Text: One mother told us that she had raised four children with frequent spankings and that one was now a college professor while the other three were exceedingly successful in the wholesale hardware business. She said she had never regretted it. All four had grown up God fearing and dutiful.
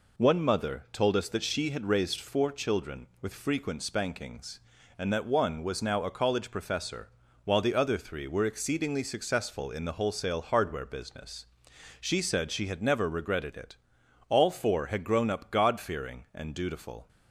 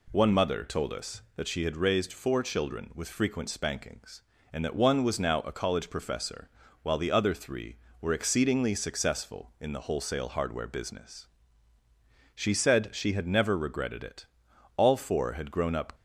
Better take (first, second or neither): first